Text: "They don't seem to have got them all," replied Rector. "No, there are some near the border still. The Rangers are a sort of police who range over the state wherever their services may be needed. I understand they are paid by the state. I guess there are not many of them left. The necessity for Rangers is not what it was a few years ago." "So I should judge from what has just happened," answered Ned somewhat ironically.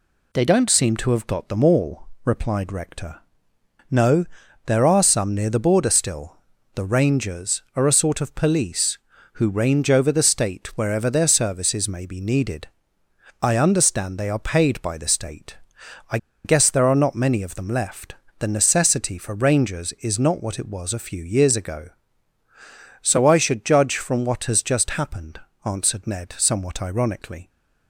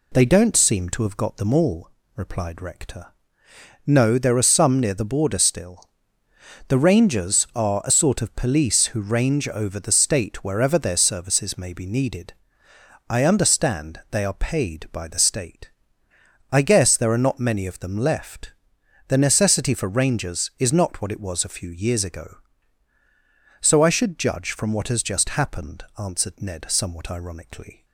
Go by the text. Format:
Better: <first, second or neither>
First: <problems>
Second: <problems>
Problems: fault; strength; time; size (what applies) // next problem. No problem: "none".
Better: second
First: pauses between "I" and "guess"; slight; at 16.1 s; 0.27 s long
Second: none